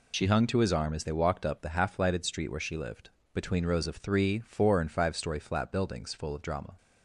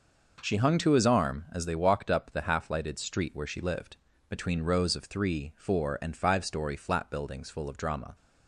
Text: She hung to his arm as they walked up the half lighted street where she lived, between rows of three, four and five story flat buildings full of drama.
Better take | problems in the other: second | loses the start of "She"; at 0.1 s; 70 ms

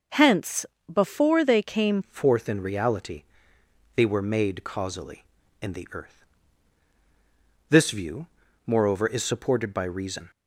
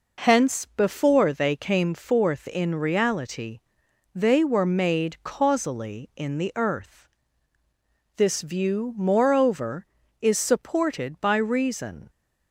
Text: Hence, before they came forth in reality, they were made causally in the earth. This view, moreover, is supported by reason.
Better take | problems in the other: second | changes voice at "forth"; from 2.0 s on; 8.3 s long

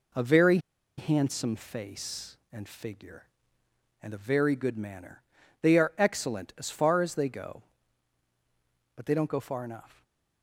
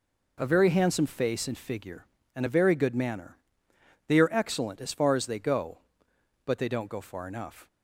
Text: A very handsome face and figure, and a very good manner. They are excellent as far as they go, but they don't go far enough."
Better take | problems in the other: second | pauses between "very" and "handsome"; at 0.5 s; 0.39 s long // stays silent after the last word; slight; from 9.9 s on; 0.5 s long

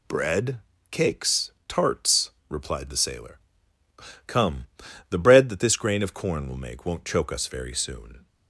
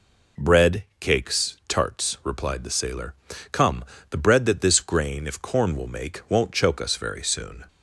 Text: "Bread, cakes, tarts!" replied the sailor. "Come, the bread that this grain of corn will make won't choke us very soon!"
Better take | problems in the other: first | says "if" for "of"; at 5.2 s

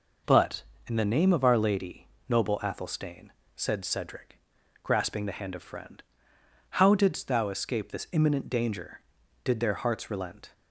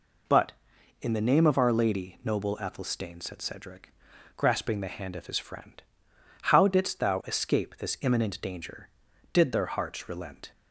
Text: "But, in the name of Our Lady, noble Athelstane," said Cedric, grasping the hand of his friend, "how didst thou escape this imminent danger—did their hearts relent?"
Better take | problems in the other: second | skips "his"; at 5.6 s

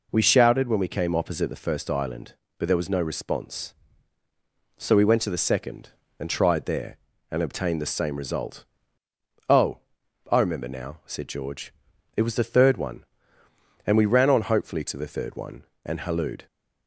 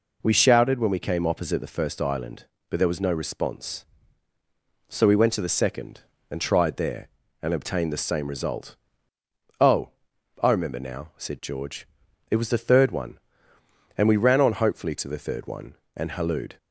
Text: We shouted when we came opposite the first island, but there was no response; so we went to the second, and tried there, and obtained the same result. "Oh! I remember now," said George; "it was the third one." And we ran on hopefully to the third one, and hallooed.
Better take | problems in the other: neither | none

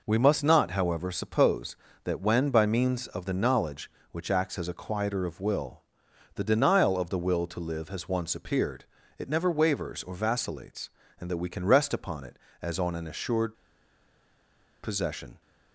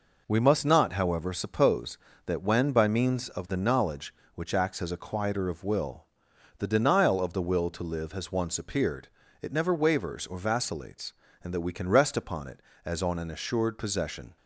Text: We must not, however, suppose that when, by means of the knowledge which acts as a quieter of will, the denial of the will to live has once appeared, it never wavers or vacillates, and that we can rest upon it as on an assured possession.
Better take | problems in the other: second | pauses between "assured" and "possession"; strong; at 13.5 s; 1.2 s long

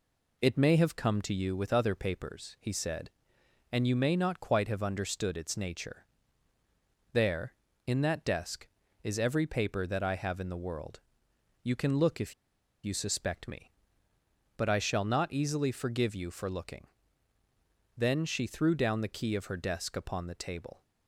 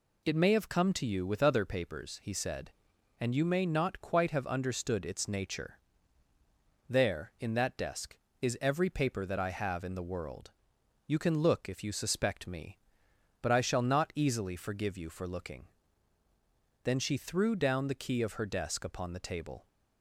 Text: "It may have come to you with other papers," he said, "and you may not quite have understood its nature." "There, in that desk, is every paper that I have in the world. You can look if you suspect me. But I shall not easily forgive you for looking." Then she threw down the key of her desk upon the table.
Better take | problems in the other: second | pauses between "if" and "you"; noticeable; at 12.3 s; 0.50 s long

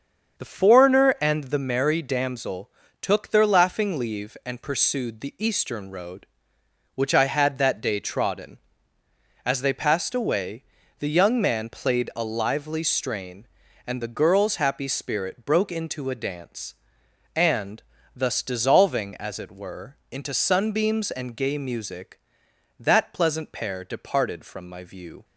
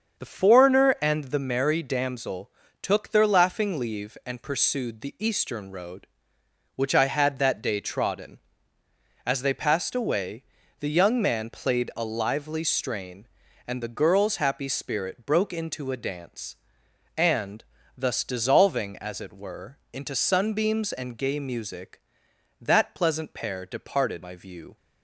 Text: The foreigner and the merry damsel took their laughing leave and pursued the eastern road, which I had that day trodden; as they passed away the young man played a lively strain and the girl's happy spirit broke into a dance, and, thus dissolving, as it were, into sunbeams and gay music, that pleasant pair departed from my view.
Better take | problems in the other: first | starts louder than the rest; until 1.2 s; 7 dB; also in the first // pauses between "damsel" and "took"; slight; at 2.4 s; 0.32 s long; slight in the first // pauses between "away" and "the"; at 10.4 s; 0.38 s long; also in the first // skips "from"; at 24.2 s

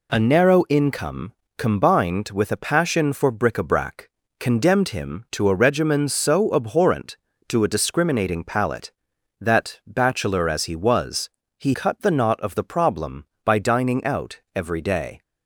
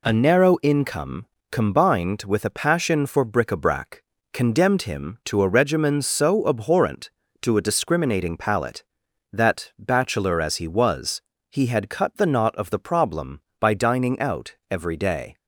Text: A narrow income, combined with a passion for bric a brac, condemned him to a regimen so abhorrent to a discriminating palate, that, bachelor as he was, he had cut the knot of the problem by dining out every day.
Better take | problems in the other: second | skips "had"; at 11.7 s

